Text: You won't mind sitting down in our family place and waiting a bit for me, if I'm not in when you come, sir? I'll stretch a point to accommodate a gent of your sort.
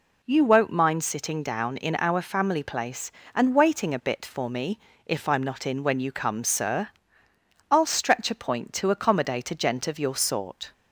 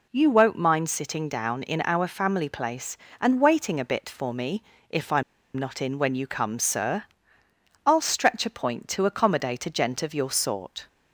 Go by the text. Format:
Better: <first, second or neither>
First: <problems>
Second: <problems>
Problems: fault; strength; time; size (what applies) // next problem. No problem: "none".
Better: first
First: none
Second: pauses between "I'm" and "not"; slight; at 5.2 s; 0.34 s long